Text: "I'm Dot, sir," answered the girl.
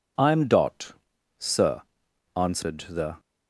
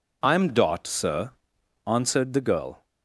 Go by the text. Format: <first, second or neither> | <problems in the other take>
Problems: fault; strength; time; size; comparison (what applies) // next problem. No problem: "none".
second | stops before "girl"; at 3.1 s